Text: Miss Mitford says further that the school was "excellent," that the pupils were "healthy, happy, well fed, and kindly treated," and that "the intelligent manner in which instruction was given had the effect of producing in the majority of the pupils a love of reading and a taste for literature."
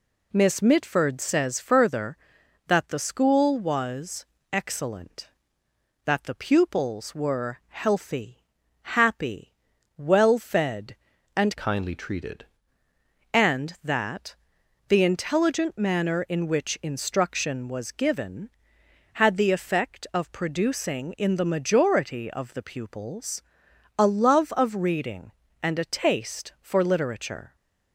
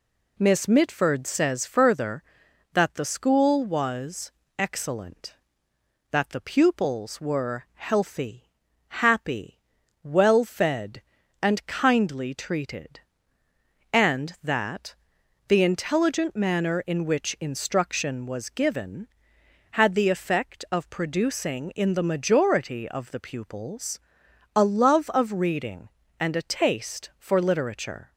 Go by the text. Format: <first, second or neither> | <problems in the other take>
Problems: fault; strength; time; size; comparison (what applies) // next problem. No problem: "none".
second | pauses between "was" and "excellent"; slight; at 4.2 s; 0.26 s long; slight in the second // changes voice from "kindly" to "treated"; from 11.5 to 12.4 s; 0.9 s long // pauses between "that" and "the"; noticeable; at 14.3 s; 0.50 s long; noticeable in the second // pauses between "pupils" and "a"; noticeable; at 23.4 s; 0.58 s long; noticeable in the second